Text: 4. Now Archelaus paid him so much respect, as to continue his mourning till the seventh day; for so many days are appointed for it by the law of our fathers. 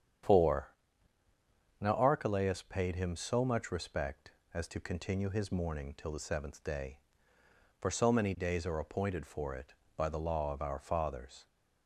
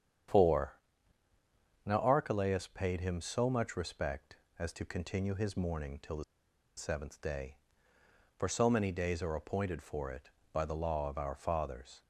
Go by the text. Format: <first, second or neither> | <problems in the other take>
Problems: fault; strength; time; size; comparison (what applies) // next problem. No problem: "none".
first | starts louder than the rest; strong; until 2.5 s; 8.5 dB; strong in the first // pauses between "the" and "seventh"; noticeable; at 6.2 s; 0.53 s long